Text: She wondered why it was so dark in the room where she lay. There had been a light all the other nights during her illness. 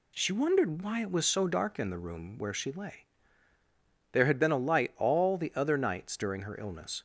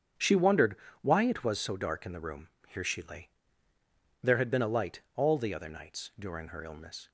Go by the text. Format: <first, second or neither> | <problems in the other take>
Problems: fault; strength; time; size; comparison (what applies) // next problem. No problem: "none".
first | starts louder than the rest; strong; until 1.4 s; 8 dB // pauses between "wondered" and "why"; slight; at 0.7 s; 0.26 s long // says "here" for "where"; at 2.6 s